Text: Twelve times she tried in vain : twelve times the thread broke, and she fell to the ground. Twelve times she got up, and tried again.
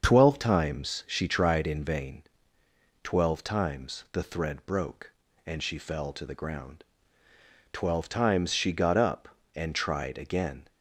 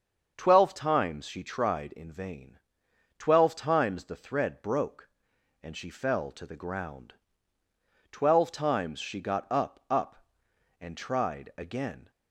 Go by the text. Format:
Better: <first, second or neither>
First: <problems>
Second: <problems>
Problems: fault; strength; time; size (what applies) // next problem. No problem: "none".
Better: first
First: starts louder than the rest; until 1.0 s; 6.5 dB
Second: starts louder than the rest; until 1.3 s; 7 dB // says "up" twice; at 9.8 s